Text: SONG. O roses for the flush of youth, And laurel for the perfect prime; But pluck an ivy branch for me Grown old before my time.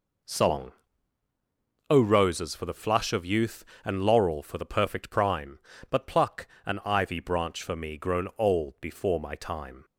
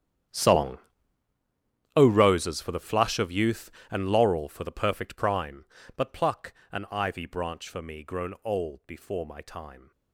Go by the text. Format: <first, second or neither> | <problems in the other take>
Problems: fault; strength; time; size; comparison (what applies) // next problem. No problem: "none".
first | gets quieter; strong; throughout; 18.5 dB // pauses between "pluck" and "an"; slight; at 6.5 s; 0.18 s long; slight in the first